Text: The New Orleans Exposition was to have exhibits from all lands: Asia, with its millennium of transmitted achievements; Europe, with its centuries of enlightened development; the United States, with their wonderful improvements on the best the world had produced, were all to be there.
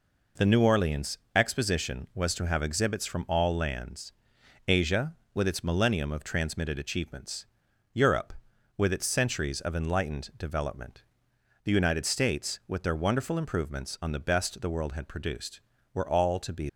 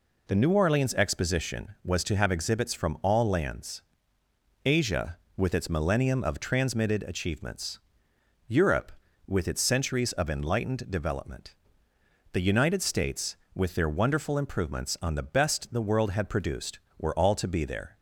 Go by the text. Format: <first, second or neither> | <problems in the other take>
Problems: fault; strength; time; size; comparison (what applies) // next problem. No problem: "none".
second | pauses between "Orleans" and "Exposition"; slight; at 1.1 s; 0.18 s long // stops before "there"; at 16.6 s